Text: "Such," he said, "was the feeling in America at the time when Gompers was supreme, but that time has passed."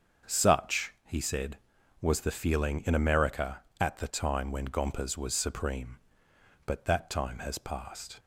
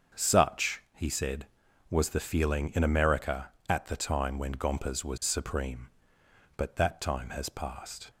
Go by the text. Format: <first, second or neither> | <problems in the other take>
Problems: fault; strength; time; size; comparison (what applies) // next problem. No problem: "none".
neither | starts louder than the rest; the same in both